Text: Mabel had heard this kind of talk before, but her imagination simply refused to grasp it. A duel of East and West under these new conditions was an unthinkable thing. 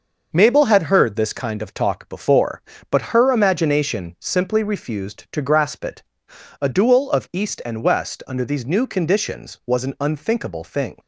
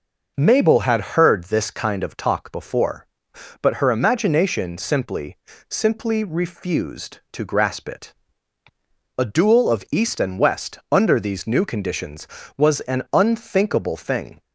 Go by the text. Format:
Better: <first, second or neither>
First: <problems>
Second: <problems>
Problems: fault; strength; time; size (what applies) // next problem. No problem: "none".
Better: first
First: none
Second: says "simply" twice; at 5.6 s